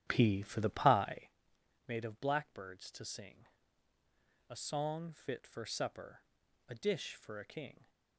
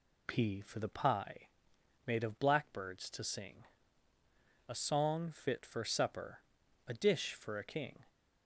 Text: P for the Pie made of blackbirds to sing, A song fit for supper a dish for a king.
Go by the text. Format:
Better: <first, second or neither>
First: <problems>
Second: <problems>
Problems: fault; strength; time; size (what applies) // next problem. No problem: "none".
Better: second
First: starts louder than the rest; strong; until 1.3 s; 10.5 dB // pauses between "Pie" and "made"; noticeable; at 1.3 s; 0.56 s long // pauses between "supper" and "a"; noticeable; at 6.2 s; 0.48 s long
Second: pauses between "Pie" and "made"; noticeable; at 1.4 s; 0.56 s long // pauses between "supper" and "a"; noticeable; at 6.3 s; 0.48 s long